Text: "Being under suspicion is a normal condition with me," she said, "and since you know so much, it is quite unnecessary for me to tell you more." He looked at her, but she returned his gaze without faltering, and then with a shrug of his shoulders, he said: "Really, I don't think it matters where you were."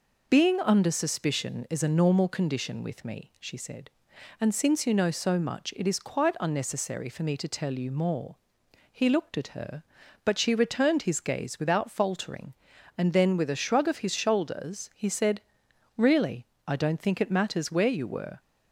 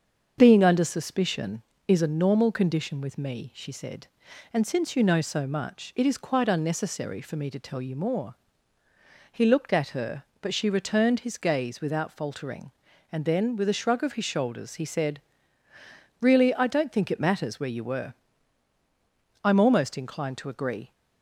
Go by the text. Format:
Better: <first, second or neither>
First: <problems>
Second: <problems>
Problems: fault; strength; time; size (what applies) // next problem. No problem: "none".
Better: first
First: none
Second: starts louder than the rest; until 1.4 s; 7 dB // goes on to say "I'm almost inclined to agree"; from 19.4 s on; 1.4 s long